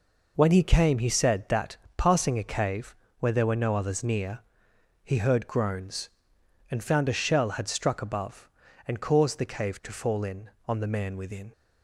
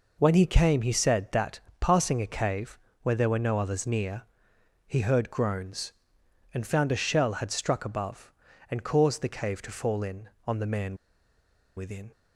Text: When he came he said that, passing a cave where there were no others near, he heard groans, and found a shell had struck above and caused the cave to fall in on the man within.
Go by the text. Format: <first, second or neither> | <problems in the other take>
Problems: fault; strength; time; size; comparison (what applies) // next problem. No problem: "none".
first | pauses between "cave" and "where"; slight; at 2.7 s; 0.26 s long; slight in the first // pauses between "man" and "within"; noticeable; at 10.9 s; 0.80 s long